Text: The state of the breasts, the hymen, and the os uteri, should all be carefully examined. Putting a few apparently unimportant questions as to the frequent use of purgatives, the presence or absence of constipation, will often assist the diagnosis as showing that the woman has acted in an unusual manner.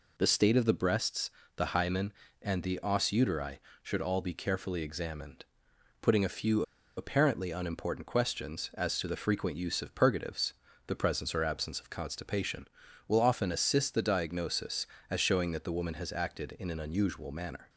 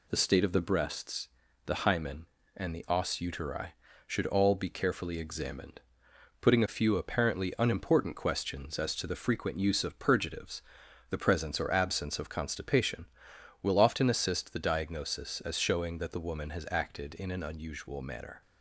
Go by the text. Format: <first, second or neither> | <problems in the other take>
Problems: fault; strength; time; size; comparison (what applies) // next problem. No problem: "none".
second | pauses between "few" and "apparently"; slight; at 6.6 s; 0.34 s long